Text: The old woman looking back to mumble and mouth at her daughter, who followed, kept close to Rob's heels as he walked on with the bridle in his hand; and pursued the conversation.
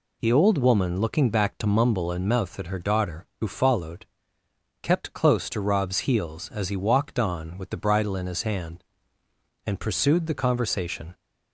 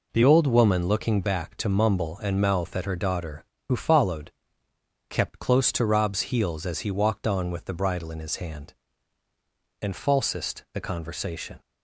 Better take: first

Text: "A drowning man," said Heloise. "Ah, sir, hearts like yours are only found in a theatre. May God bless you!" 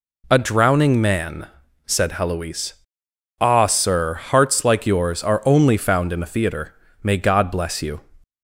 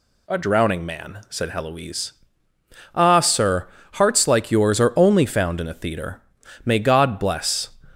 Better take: first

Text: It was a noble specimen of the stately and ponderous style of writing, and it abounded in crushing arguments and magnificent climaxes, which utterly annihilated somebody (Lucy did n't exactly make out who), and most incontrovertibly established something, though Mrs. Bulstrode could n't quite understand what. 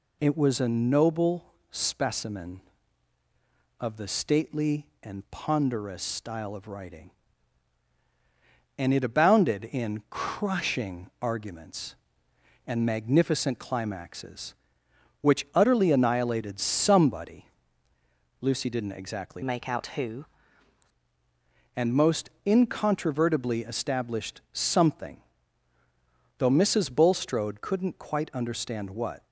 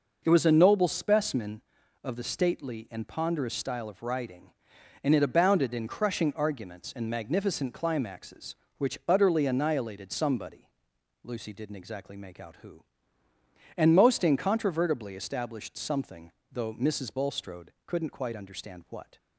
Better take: second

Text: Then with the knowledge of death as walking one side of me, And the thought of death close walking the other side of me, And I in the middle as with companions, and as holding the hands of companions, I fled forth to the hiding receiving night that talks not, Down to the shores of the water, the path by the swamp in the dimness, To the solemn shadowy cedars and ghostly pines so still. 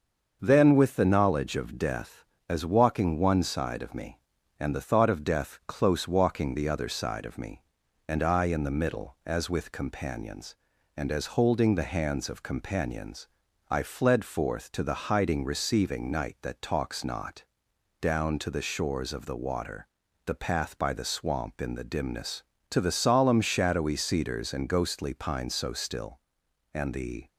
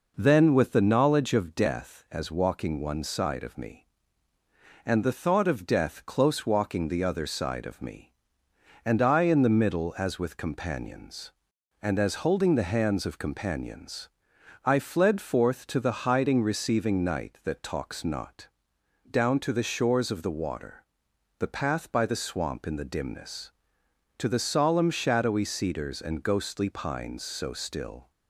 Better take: second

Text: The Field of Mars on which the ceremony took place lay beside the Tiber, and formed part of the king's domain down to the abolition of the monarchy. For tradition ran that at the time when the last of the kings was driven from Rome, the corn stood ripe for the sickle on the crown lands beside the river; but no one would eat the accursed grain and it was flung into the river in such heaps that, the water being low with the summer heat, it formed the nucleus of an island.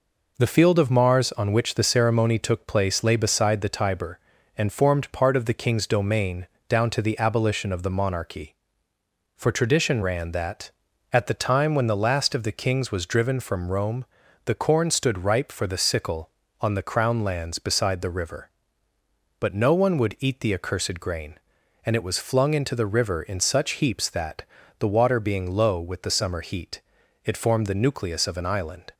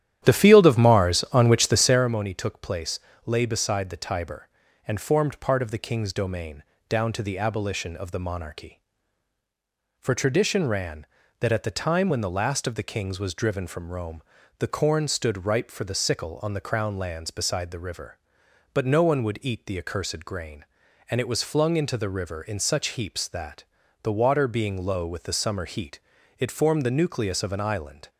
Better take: first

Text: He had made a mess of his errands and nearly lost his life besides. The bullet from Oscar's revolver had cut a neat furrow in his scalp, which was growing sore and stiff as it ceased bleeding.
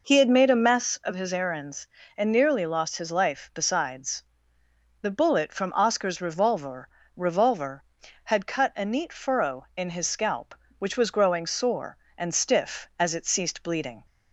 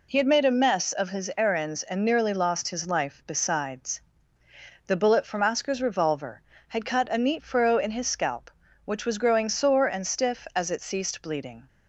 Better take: second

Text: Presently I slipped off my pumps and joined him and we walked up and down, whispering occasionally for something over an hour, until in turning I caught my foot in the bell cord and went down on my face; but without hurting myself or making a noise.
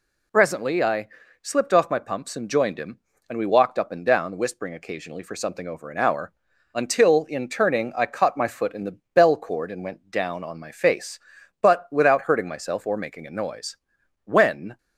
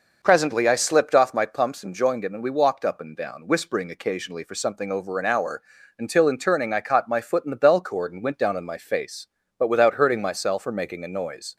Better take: second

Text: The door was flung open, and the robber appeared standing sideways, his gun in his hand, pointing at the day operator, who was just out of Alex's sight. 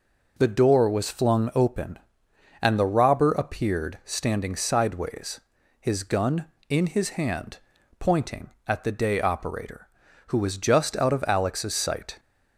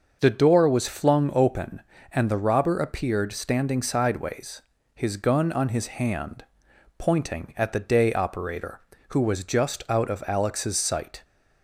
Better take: first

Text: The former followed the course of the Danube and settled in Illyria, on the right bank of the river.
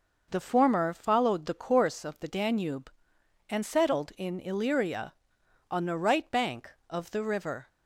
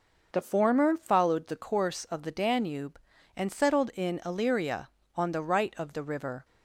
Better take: first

